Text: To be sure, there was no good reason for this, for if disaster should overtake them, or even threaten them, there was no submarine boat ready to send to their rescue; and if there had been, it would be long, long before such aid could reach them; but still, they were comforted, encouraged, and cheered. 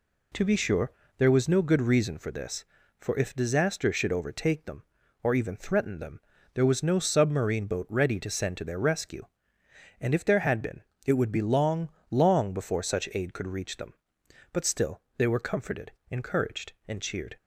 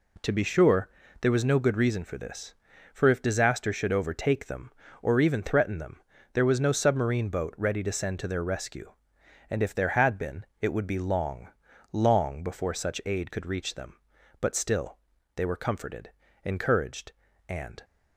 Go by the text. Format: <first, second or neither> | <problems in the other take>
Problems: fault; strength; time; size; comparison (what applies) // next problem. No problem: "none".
first | stops before "cheered"; at 17.8 s